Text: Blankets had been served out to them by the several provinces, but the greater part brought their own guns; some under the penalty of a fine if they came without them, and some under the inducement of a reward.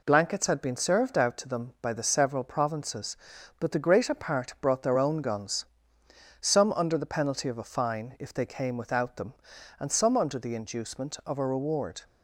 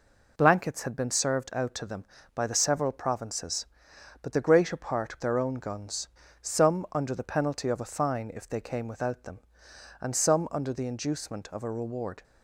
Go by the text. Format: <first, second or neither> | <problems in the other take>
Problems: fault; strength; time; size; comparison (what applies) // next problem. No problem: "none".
first | skips "brought"; at 5.2 s